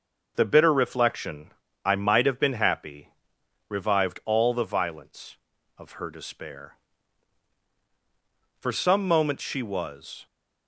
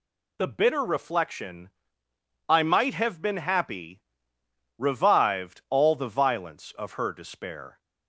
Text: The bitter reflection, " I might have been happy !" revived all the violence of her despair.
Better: second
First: goes on to say "For some moments she was"; strong; from 8.5 s on; 1.6 s long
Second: none

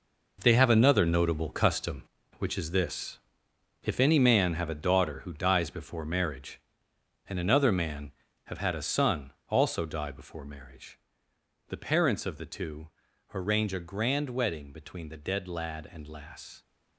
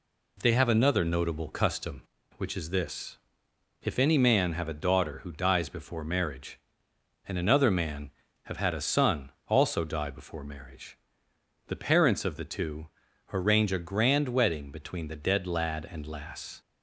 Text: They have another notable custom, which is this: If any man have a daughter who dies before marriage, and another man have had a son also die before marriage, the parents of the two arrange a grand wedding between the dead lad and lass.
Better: second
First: gets quieter; strong; throughout; 10.5 dB // pauses between "son" and "also"; slight; at 9.3 s; 0.16 s long // pauses between "two" and "arrange"; noticeable; at 12.8 s; 0.46 s long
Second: pauses between "son" and "also"; slight; at 9.3 s; 0.16 s long // pauses between "two" and "arrange"; noticeable; at 12.8 s; 0.46 s long

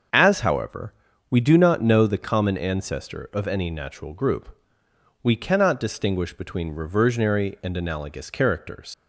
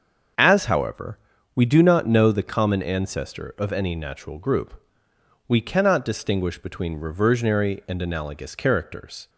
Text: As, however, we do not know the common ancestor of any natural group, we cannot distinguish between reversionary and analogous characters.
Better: second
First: starts louder than the rest; until 1.5 s; 6.5 dB // leaves "characters" unfinished; at 8.9 s; 100 ms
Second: starts louder than the rest; until 1.7 s; 7 dB

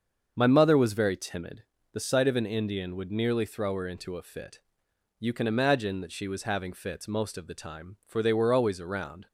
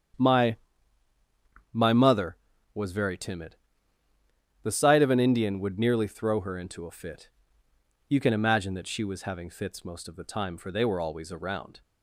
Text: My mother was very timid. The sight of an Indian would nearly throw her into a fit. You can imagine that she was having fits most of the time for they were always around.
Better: first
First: starts louder than the rest; until 1.3 s; 7 dB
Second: starts louder than the rest; strong; until 2.3 s; 8.5 dB // says "My" twice; at 1.7 s

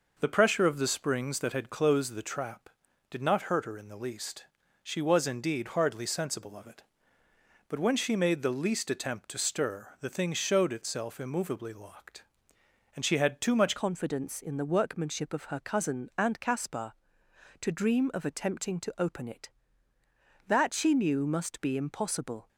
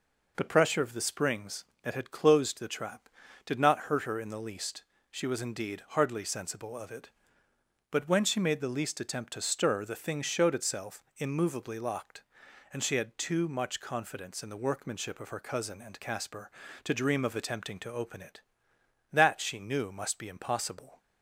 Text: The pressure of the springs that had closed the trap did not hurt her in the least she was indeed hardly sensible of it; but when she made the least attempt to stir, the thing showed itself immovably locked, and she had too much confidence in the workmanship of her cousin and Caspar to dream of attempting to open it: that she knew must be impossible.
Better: second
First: pauses between "least" and "she"; at 4.4 s; 0.38 s long // changes voice at "confidence"; from 13.7 s on; 8.7 s long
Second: pauses between "least" and "she"; slight; at 4.8 s; 0.28 s long

